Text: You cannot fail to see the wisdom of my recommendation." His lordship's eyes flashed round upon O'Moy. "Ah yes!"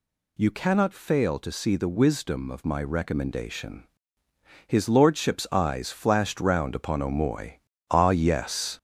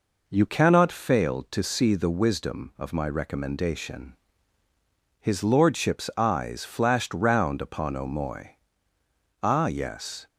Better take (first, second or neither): second